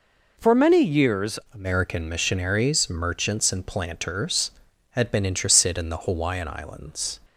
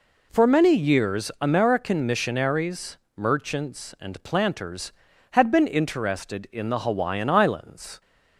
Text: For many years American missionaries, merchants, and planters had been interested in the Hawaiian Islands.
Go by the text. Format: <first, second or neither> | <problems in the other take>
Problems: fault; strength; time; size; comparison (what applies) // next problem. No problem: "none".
second | changes voice at "American"; from 1.5 s on; 5.6 s long